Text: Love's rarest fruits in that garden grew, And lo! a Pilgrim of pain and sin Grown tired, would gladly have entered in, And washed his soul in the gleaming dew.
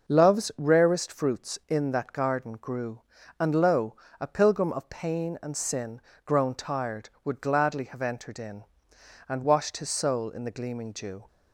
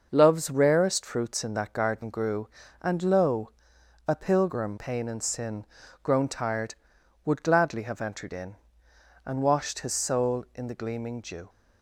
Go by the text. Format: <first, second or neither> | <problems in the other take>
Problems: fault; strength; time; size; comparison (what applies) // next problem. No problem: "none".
first | starts louder than the rest; noticeable; until 1.1 s; 6 dB; also in the first // skips "of"; at 4.7 s // pauses between "sin" and "Grown"; at 5.6 s; 0.38 s long; slight in the first